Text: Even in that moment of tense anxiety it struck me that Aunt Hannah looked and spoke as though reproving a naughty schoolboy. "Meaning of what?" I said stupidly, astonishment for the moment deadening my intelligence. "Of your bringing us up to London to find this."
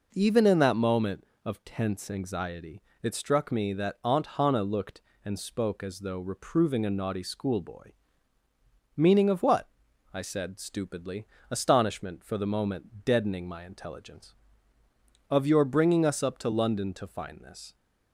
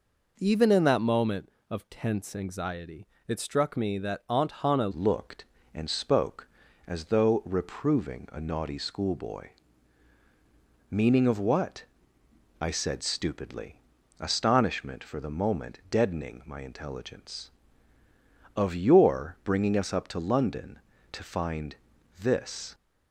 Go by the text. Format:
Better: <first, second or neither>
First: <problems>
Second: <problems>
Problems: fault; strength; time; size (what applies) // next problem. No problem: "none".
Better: first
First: pauses between "anxiety" and "it"; slight; at 2.8 s; 0.20 s long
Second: pauses between "anxiety" and "it"; slight; at 3.0 s; 0.20 s long // changes voice at "looked"; from 4.9 s on; 17.8 s long // pauses between "find" and "this"; at 21.7 s; 0.42 s long